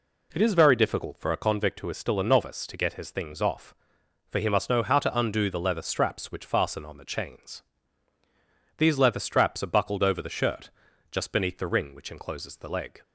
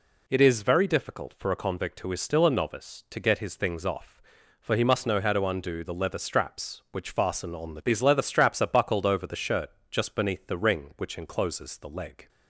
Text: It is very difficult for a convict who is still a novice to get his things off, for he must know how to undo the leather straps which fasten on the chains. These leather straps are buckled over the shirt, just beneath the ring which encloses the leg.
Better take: first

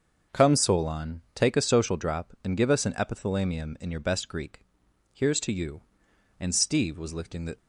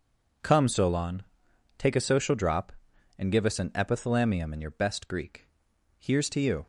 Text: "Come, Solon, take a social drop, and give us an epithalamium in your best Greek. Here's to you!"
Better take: second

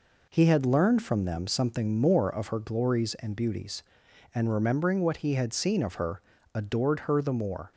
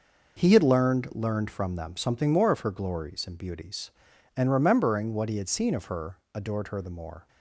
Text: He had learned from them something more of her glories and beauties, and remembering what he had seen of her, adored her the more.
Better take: first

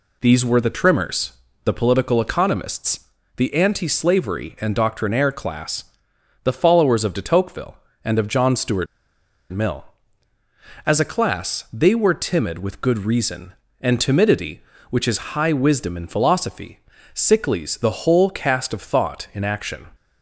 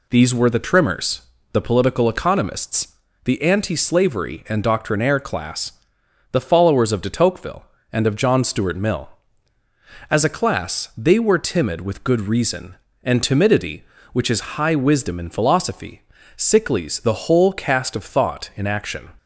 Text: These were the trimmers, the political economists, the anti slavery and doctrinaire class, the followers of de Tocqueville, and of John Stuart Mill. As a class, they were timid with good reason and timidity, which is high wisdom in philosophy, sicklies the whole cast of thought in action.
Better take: second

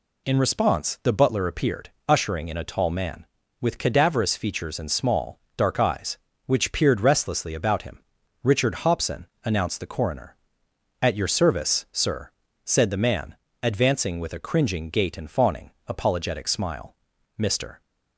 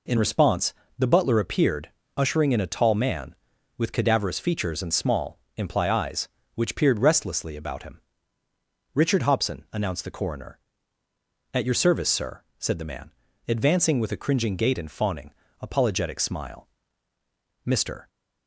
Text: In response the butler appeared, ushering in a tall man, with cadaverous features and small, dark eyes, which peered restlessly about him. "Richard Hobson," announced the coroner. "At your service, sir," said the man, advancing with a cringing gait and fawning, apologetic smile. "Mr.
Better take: first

